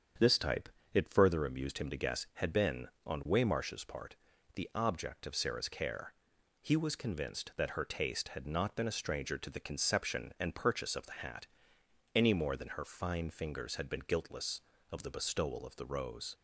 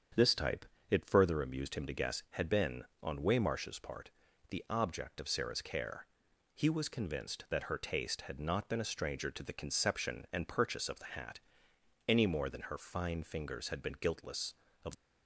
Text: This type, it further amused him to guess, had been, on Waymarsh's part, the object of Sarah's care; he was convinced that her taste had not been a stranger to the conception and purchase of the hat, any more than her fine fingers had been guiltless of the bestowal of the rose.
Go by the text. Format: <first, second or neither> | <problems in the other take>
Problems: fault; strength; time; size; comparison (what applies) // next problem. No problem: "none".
first | starts louder than the rest; strong; until 1.3 s; 7.5 dB; strong in the first // stops before "the bestowal of the rose"; at 14.9 s